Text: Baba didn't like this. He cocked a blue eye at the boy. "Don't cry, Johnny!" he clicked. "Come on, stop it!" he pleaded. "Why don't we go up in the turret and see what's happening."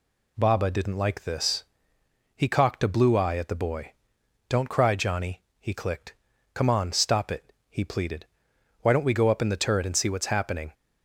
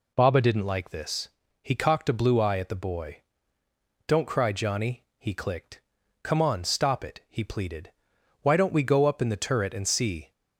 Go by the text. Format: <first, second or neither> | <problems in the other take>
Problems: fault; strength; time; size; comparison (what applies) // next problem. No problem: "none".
first | stops before "what's happening"; at 10.3 s